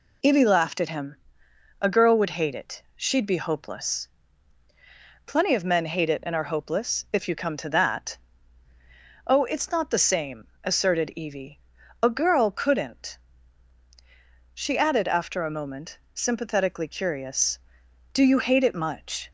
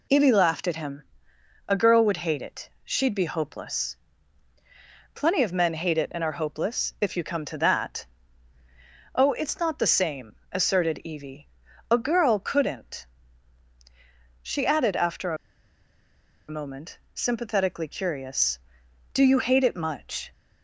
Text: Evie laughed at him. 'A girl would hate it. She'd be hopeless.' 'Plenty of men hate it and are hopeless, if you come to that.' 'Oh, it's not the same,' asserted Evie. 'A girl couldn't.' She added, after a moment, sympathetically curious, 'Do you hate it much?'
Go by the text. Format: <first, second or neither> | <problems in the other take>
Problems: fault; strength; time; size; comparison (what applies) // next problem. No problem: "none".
first | pauses between "after" and "a"; at 15.3 s; 1.1 s long